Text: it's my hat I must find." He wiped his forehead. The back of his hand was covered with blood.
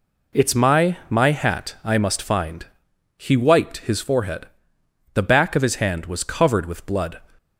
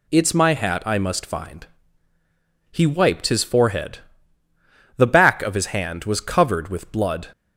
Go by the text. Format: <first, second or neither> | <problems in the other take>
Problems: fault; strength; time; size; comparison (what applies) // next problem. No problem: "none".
second | says "my" twice; at 1.0 s